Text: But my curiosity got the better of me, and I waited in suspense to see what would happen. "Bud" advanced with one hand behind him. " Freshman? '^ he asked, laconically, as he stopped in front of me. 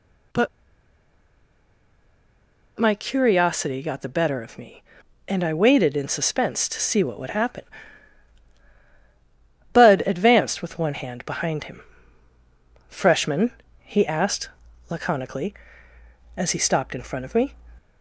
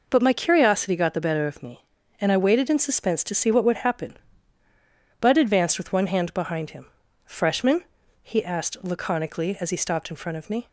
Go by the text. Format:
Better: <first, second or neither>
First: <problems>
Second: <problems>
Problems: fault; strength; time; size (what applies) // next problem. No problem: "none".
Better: second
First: pauses between "But" and "my"; strong; at 0.4 s; 2.3 s long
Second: none